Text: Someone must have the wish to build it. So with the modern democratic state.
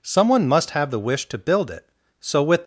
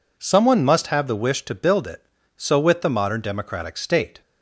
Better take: second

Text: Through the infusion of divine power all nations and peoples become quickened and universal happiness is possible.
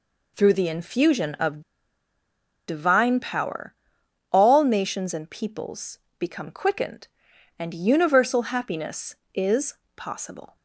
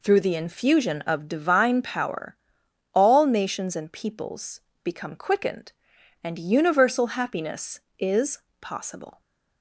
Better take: second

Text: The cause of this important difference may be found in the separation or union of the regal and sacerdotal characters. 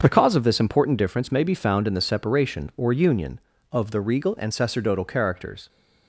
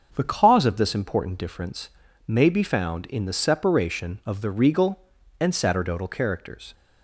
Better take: first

